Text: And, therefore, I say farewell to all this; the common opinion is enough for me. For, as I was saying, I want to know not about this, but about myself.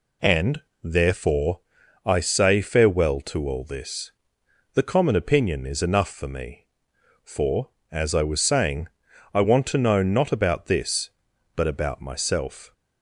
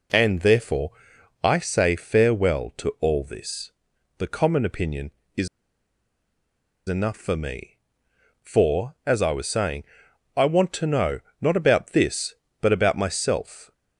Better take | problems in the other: first | pauses between "is" and "enough"; strong; at 5.4 s; 1.3 s long // pauses between "know" and "not"; slight; at 11.1 s; 0.22 s long

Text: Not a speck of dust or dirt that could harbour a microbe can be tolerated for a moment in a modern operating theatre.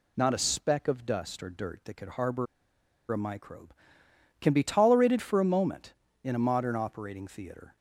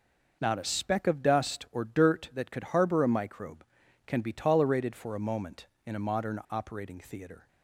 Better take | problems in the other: second | pauses between "harbour" and "a"; noticeable; at 2.4 s; 0.66 s long

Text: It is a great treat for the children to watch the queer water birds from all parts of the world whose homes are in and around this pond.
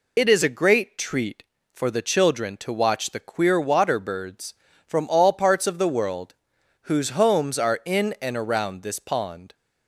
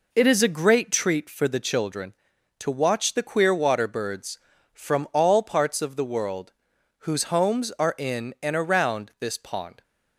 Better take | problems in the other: second | loses the start of "It"; at 0.1 s; 50 ms // pauses between "world" and "whose"; noticeable; at 6.3 s; 0.48 s long; noticeable in the second

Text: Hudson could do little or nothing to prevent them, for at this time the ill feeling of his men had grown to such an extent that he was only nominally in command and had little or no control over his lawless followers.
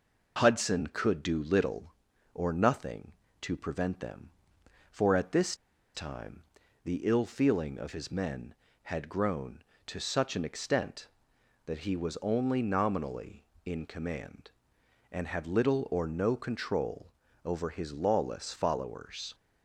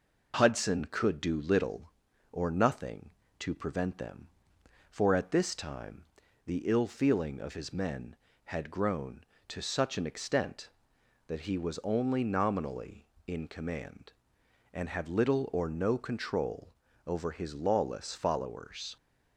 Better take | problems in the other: second | pauses between "this" and "time"; at 5.5 s; 0.39 s long // pauses between "time" and "the"; at 6.4 s; 0.40 s long; also in the second // pauses between "control" and "over"; at 17.0 s; 0.38 s long; also in the second

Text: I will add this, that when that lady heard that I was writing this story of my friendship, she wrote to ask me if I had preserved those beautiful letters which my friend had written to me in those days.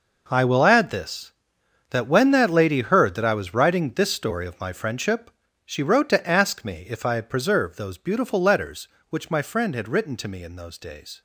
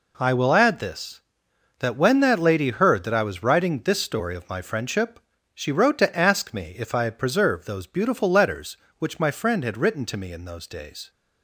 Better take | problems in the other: second | gets quieter; strong; throughout; 14.5 dB

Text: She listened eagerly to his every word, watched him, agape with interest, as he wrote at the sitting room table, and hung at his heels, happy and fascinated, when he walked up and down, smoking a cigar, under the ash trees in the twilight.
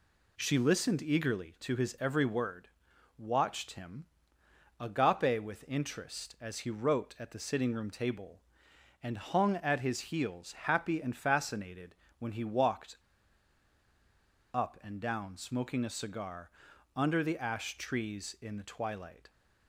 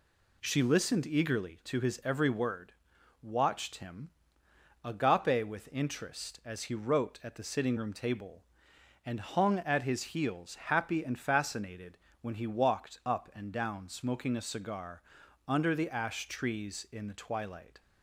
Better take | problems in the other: second | pauses between "walked" and "up"; strong; at 12.9 s; 1.5 s long

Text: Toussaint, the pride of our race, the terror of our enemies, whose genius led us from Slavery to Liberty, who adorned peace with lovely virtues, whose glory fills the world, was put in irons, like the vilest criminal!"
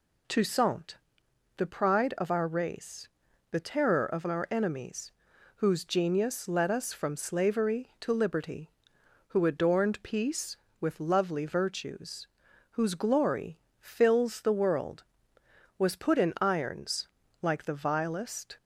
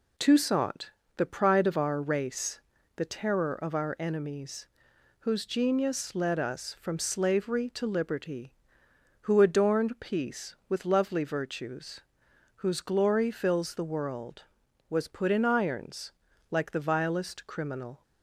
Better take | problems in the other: second | pauses between "glory" and "fills"; slight; at 13.5 s; 0.20 s long // stops before "criminal"; at 18.5 s

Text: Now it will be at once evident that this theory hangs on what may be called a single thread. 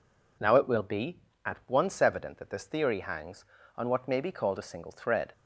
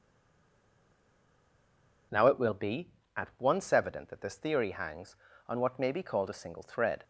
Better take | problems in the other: first | stays silent before the first word; until 2.1 s; 2.1 s long

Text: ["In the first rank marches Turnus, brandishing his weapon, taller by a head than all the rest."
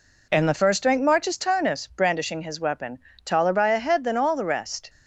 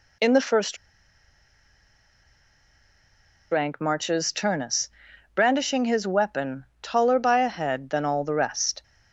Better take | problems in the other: first | pauses between "first" and "rank"; strong; at 0.7 s; 2.7 s long

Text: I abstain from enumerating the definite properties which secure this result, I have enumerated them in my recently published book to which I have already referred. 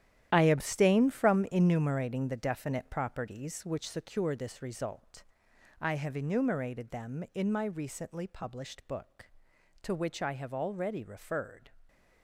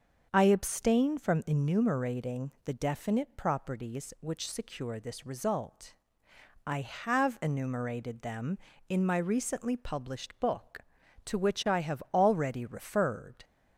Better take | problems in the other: second | gets quieter; strong; throughout; 11.5 dB // starts louder than the rest; strong; until 1.3 s; 11.5 dB; also in the second

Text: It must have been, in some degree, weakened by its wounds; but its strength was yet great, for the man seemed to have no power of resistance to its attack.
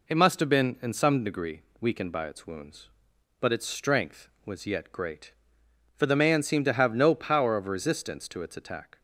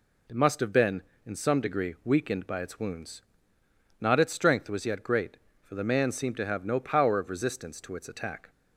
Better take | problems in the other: first | says "not" for "but"; at 3.9 s

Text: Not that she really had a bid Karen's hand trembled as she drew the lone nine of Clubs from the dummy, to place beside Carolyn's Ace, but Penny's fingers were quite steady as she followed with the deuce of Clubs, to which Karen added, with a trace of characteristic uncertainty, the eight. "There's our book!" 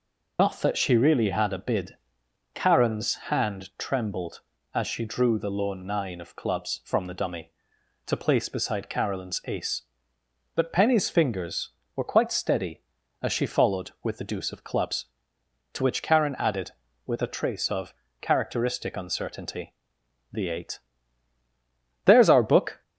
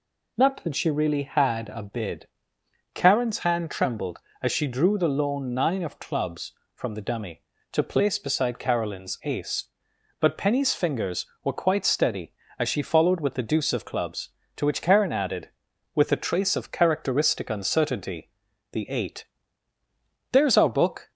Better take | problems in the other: second | loses the start of "Not"; at 0.3 s; 95 ms // pauses between "bid" and "Karen's"; noticeable; at 1.9 s; 0.58 s long; noticeable in the second // pauses between "of" and "characteristic"; slight; at 17.9 s; 0.26 s long

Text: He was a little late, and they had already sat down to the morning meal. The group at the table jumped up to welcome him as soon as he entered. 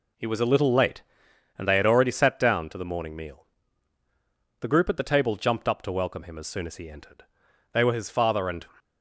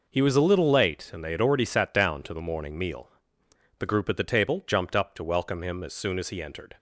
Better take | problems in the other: second | goes on to say "They were his father and"; noticeable; from 7.7 s on; 0.92 s long

